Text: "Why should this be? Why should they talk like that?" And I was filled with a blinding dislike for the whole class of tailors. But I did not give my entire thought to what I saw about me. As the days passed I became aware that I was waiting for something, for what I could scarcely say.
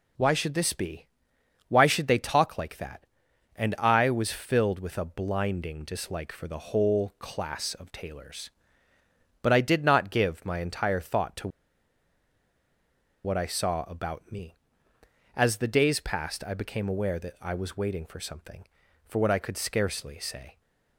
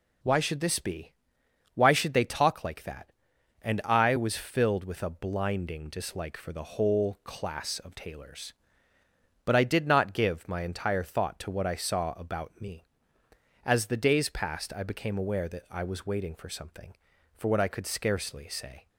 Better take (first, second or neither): second